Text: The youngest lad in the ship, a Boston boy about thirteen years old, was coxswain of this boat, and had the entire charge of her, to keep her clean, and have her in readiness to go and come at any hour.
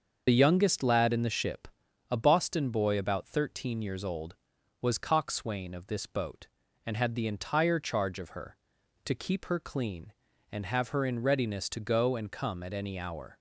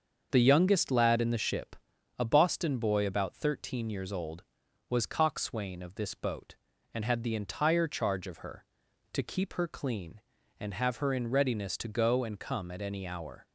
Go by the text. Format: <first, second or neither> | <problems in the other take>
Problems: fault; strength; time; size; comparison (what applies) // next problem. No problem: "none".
second | loses the start of "The"; at 0.2 s; 35 ms // starts louder than the rest; until 1.2 s; 6.5 dB; also in the second